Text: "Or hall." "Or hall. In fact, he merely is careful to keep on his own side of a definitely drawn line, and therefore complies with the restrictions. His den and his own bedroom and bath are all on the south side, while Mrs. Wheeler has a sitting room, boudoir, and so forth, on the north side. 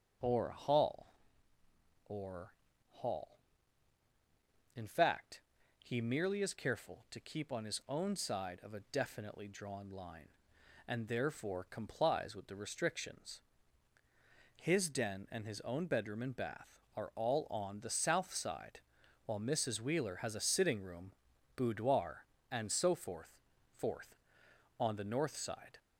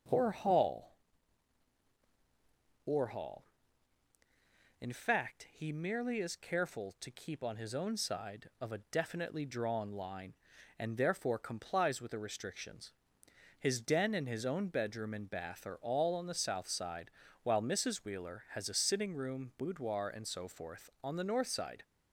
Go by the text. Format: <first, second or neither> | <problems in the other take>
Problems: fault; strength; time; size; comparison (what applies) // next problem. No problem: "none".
second | starts louder than the rest; strong; until 2.1 s; 7 dB // pauses between "Or" and "hall"; slight; at 2.5 s; 0.34 s long // says "forth" twice; at 23.7 s